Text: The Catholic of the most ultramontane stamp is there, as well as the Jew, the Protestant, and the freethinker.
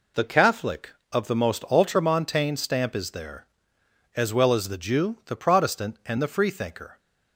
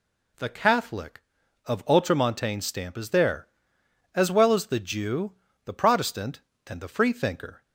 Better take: first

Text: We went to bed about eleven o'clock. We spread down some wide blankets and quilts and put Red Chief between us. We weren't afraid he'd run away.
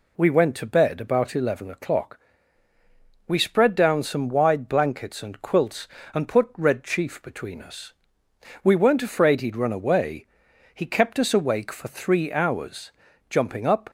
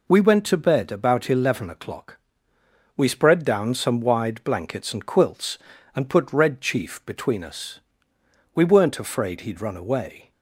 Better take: second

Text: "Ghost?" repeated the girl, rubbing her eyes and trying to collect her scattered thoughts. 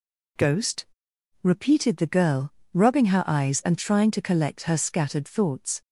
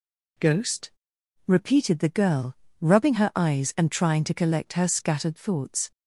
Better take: neither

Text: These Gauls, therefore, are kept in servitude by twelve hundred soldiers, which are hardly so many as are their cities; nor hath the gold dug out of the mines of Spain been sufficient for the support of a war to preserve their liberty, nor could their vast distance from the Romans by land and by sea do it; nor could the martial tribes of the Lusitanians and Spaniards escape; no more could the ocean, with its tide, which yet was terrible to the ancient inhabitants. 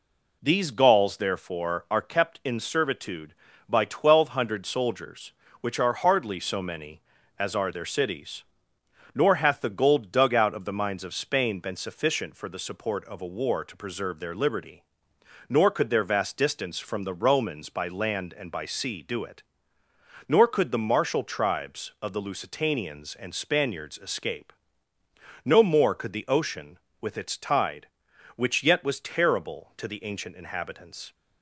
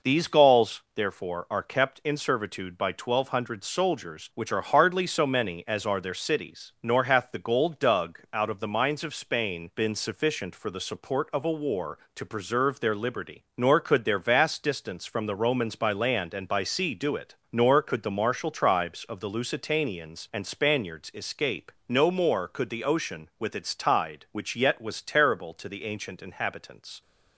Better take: neither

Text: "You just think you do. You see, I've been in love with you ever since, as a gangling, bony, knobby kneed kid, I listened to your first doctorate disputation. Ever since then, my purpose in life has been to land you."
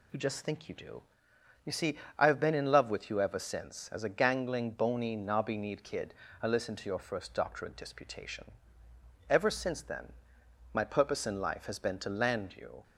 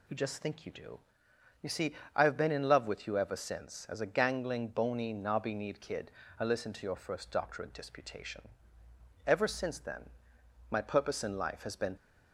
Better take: first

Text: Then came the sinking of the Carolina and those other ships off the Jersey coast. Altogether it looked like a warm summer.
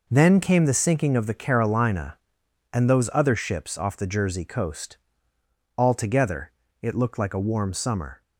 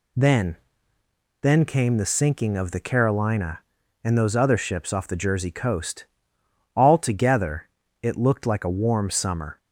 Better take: first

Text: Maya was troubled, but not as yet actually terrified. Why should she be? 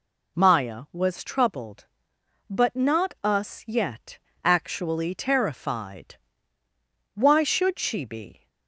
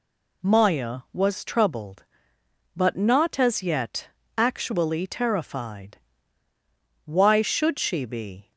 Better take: second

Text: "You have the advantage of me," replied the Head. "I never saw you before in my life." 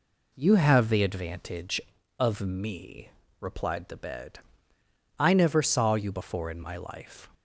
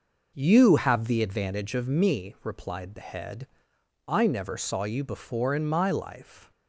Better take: second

